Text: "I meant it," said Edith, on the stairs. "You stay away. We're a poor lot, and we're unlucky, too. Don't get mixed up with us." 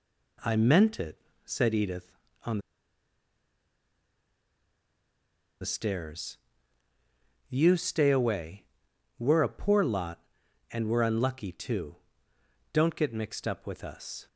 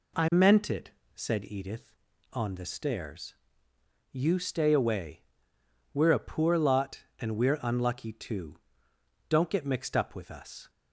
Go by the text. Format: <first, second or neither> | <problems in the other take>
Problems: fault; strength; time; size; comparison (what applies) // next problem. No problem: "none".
second | pauses between "on" and "the"; strong; at 2.5 s; 3.0 s long